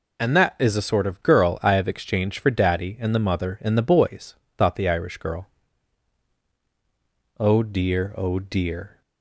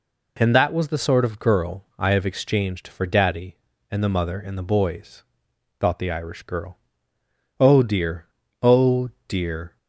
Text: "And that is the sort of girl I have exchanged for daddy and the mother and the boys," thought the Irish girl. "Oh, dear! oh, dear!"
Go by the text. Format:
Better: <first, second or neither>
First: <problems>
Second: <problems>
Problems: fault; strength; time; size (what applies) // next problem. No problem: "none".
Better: first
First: none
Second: says "was" for "is"; at 0.7 s